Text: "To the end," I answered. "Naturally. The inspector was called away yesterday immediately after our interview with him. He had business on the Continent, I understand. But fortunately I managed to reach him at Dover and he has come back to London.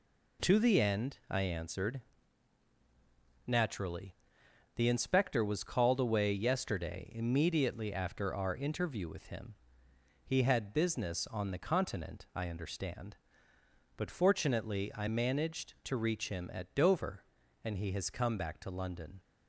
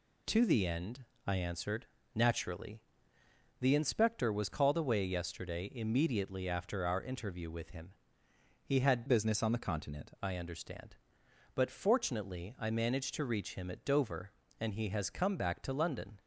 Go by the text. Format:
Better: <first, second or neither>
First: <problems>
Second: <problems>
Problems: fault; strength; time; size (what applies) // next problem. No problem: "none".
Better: first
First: none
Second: changes voice from "business" to "Continent"; from 9.0 to 10.1 s; 1.1 s long